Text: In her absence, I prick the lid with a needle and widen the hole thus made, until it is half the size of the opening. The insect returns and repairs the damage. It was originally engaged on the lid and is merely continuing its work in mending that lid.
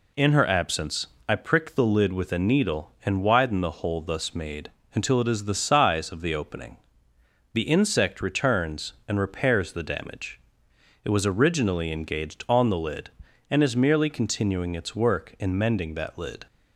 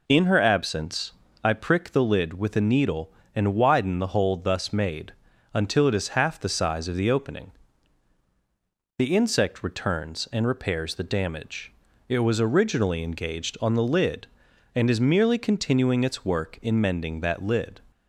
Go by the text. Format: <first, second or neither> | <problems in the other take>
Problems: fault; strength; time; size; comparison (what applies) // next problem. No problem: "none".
second | skips "half"; at 5.4 s